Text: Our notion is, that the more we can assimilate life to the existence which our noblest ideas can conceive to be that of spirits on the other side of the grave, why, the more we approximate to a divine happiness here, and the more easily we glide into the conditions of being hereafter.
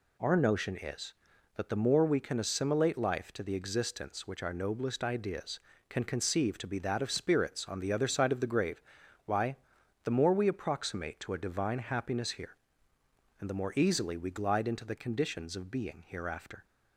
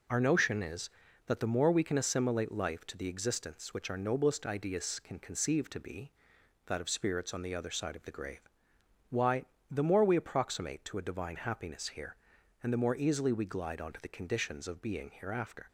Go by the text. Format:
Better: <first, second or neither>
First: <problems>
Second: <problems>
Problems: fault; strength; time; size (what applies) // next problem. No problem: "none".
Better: first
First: none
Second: says "onto" for "into"; at 13.8 s